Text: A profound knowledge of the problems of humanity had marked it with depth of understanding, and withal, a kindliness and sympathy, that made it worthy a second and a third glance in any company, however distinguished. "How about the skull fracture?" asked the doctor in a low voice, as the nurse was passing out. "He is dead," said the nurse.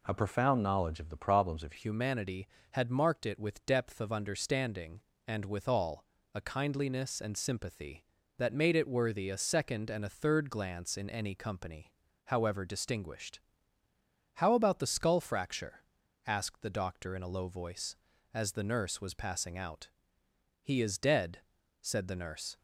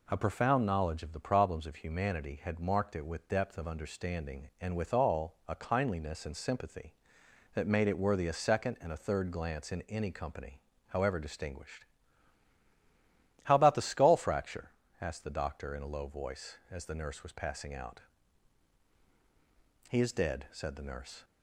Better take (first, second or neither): second